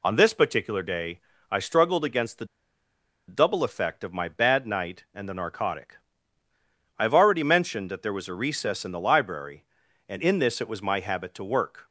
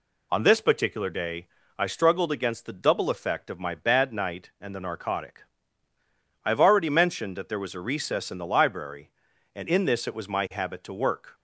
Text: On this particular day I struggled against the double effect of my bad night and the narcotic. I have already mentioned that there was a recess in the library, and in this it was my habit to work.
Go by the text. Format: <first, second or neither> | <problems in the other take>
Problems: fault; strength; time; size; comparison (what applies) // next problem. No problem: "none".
second | pauses between "day" and "I"; slight; at 1.2 s; 0.30 s long; slight in the second // pauses between "the" and "double"; noticeable; at 2.4 s; 0.83 s long